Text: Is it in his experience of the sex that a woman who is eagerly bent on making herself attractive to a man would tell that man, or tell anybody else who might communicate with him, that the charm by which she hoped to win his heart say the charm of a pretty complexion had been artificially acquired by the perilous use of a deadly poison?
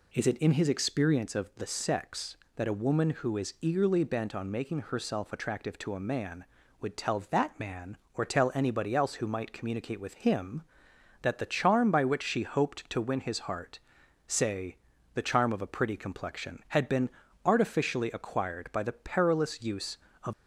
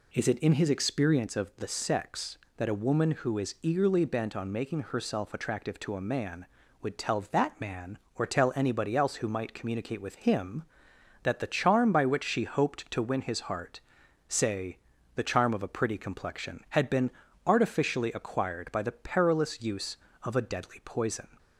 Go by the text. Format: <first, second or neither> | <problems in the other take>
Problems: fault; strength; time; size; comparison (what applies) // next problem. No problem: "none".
second | pauses between "heart" and "say"; noticeable; at 13.8 s; 0.46 s long; noticeable in the second // pauses between "say" and "the"; at 14.7 s; 0.38 s long; also in the second // pauses between "been" and "artificially"; slight; at 17.1 s; 0.34 s long; slight in the second // stops before "a deadly poison"; at 20.3 s